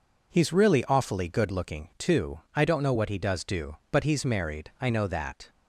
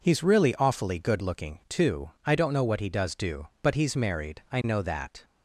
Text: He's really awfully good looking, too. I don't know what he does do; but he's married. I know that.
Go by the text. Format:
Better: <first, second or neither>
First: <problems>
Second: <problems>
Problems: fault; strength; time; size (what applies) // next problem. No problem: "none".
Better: neither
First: none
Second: none